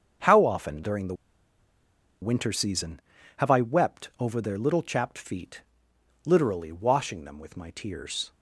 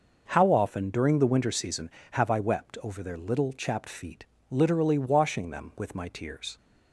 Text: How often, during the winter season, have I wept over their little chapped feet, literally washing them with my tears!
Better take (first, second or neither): second